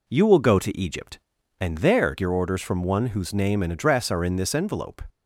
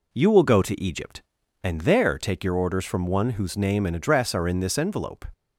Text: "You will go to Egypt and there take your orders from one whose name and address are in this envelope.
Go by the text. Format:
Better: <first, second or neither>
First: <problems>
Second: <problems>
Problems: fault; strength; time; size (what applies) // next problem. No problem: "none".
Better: second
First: skips "take"; at 2.1 s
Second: none